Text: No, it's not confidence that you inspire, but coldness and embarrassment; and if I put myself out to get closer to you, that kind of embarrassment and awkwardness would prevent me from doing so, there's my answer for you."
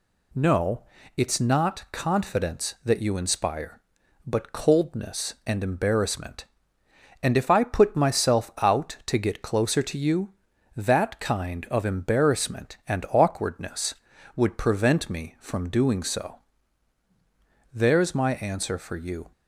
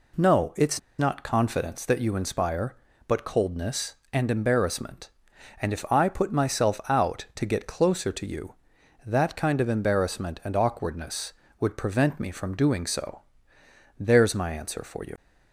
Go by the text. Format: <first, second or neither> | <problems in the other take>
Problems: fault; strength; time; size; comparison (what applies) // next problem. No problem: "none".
first | pauses between "it's" and "not"; slight; at 0.7 s; 0.20 s long